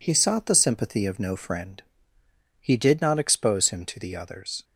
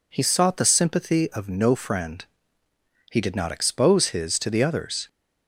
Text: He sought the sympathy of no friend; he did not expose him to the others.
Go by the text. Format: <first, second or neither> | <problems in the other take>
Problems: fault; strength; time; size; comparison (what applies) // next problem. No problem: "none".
first | says "his" for "him"; at 4.0 s